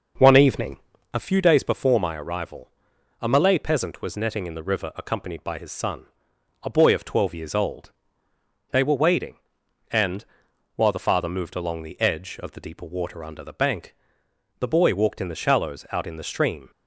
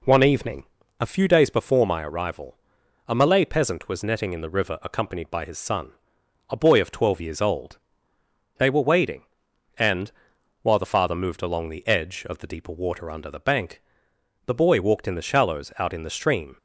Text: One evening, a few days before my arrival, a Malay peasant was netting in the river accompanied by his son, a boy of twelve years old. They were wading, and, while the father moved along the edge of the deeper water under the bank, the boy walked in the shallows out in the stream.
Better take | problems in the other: second | starts louder than the rest; noticeable; until 1.1 s; 6 dB

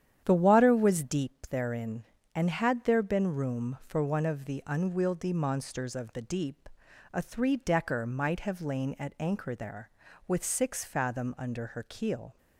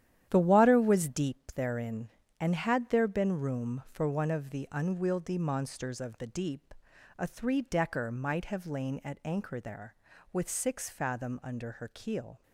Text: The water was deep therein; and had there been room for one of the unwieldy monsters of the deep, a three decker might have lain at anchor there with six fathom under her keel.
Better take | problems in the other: first | gets quieter; strong; throughout; 9.5 dB // starts louder than the rest; strong; until 1.3 s; 11 dB; strong in the first

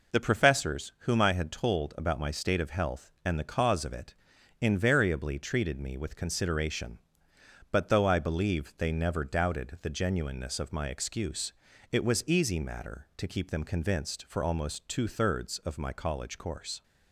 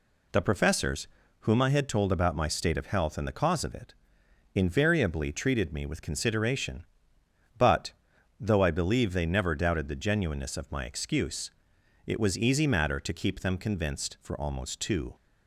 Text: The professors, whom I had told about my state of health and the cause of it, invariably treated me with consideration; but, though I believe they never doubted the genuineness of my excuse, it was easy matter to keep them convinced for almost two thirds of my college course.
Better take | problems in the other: first | stops before "thirds of my college course"; at 15.1 s

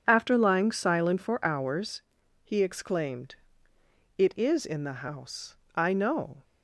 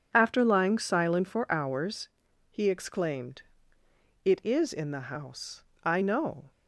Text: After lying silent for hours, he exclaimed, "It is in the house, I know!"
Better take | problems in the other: neither | none

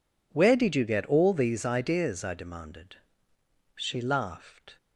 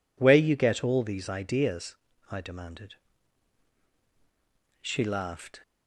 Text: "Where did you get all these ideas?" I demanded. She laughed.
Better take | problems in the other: first | skips "did"; at 0.3 s

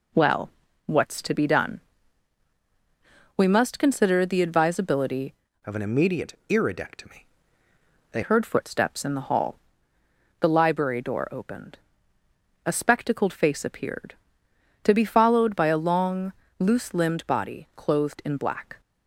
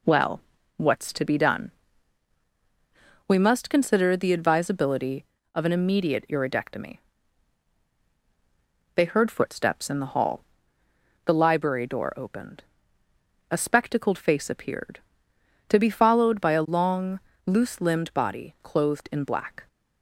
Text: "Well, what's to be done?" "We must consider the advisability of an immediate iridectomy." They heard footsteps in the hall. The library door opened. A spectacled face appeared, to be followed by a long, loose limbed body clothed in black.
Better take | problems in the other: second | changes voice from "of" to "They"; from 5.6 to 8.2 s; 2.6 s long

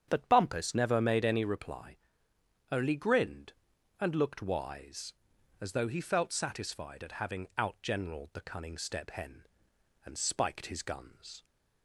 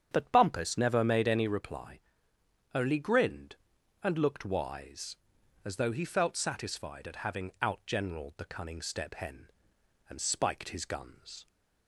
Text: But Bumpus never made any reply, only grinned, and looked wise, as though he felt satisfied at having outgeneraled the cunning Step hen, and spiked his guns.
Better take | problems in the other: neither | starts louder than the rest; strong; the same in both

